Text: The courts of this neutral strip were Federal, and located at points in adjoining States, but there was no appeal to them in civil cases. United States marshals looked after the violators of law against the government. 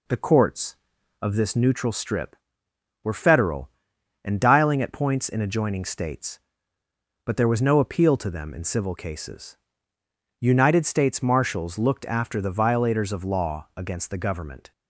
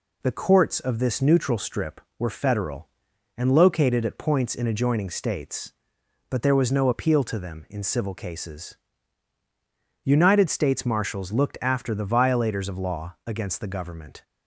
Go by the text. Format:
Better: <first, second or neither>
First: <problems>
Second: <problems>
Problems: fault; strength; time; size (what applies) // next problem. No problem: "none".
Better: second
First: says "dialing" for "located"; at 4.3 s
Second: none